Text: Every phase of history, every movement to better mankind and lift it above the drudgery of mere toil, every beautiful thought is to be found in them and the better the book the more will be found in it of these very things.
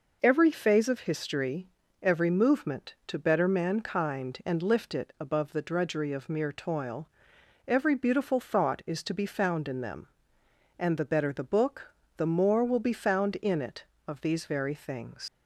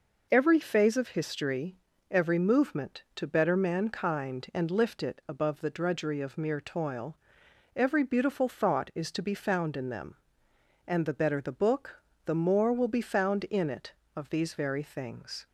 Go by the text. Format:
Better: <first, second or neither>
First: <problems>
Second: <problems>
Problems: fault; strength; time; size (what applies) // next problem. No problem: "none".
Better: second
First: pauses between "book" and "the"; slight; at 11.9 s; 0.24 s long // leaves "things" unfinished; at 15.2 s; 95 ms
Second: pauses between "book" and "the"; slight; at 12.0 s; 0.24 s long